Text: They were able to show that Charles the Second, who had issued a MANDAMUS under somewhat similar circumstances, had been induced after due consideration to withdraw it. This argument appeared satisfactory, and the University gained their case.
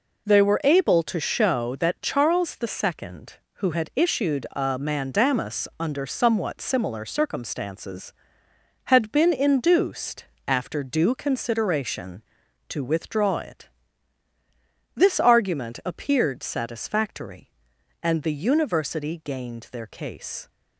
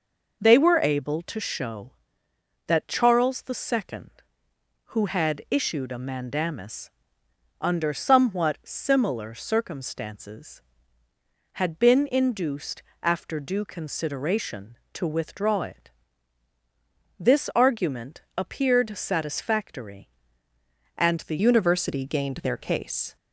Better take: first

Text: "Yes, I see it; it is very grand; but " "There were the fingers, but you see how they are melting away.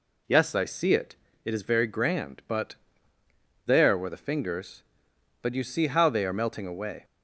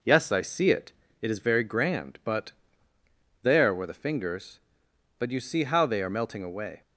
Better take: second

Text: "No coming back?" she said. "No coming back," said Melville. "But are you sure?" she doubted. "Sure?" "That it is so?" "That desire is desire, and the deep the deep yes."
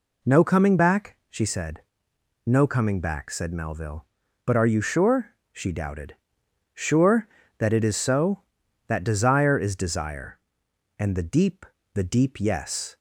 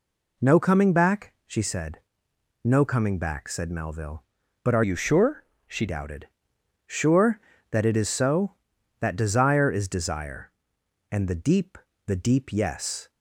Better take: first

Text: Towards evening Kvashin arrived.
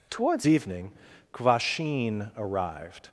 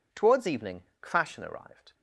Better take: second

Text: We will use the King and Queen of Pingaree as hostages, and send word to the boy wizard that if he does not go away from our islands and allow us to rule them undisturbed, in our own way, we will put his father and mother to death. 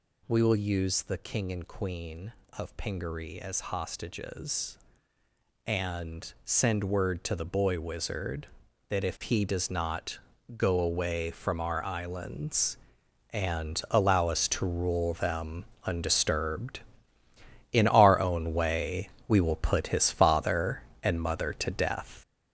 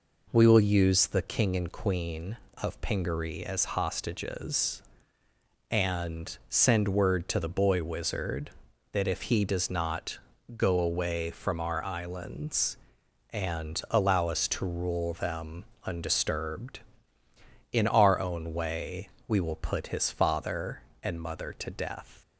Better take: second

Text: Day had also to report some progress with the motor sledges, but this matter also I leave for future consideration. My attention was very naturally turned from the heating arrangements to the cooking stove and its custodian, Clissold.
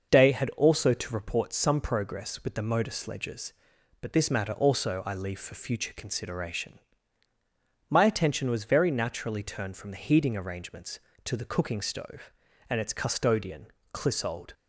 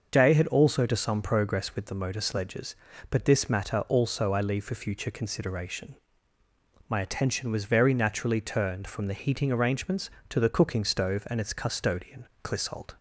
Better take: first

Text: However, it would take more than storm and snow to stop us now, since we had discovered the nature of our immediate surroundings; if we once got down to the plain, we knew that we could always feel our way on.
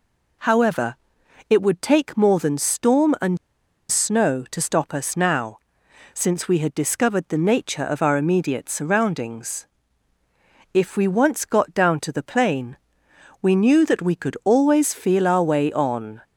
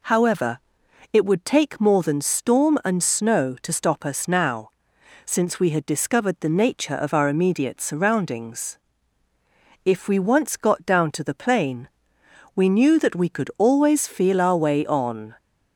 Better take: second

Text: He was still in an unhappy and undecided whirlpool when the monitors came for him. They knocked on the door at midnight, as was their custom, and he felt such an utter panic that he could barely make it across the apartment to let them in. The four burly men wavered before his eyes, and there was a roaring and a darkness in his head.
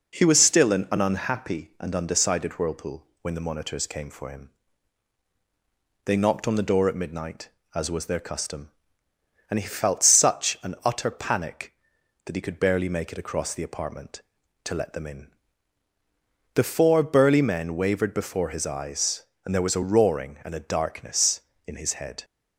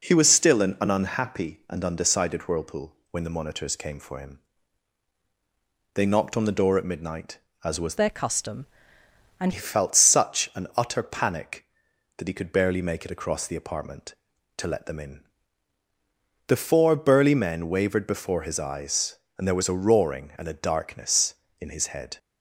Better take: first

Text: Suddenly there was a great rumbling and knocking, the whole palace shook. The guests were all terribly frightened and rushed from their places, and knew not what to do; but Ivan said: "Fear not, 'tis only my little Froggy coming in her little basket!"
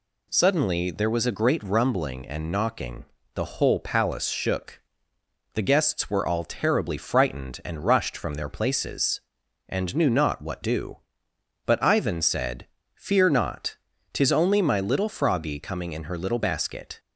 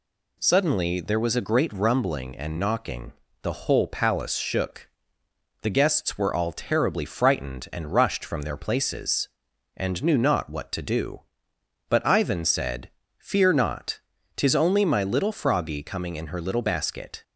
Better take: second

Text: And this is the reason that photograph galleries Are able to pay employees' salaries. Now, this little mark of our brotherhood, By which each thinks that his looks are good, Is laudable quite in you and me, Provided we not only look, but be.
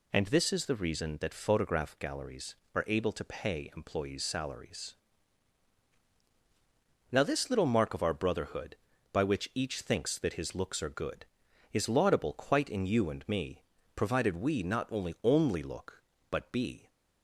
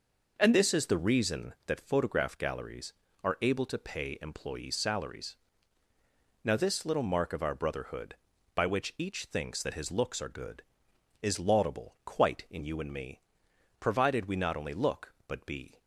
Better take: second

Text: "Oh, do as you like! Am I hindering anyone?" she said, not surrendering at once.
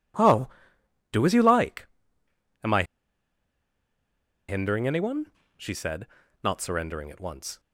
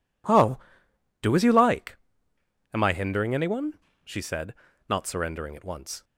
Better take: second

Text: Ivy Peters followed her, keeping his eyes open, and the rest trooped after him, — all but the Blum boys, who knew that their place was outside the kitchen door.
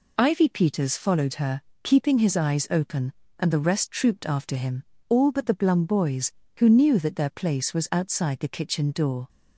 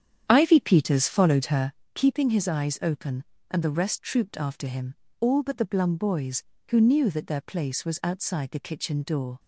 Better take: first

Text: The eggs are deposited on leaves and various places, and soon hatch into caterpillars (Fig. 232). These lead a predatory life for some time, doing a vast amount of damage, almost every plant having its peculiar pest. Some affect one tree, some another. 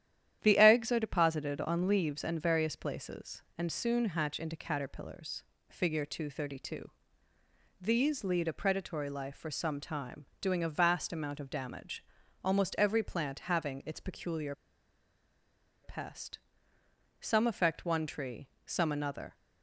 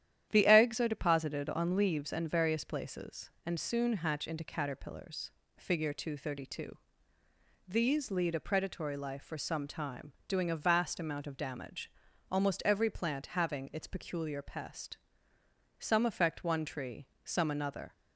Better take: second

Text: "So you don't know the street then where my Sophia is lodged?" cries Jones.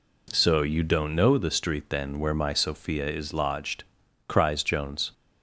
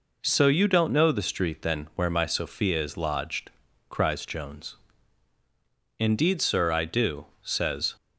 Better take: first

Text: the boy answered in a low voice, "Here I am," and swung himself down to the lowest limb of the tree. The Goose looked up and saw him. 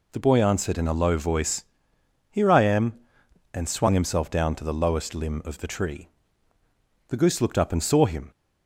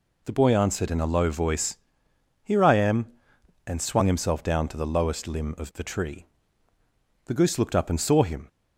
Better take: neither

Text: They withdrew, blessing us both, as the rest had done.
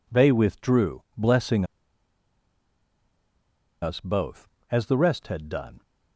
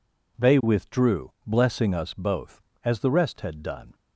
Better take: second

